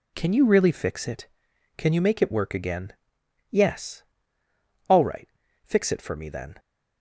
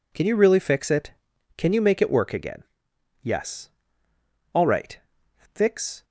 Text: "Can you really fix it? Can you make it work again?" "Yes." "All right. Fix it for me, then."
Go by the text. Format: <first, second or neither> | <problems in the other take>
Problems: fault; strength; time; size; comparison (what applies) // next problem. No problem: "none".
first | stops before "it for me then"; at 6.0 s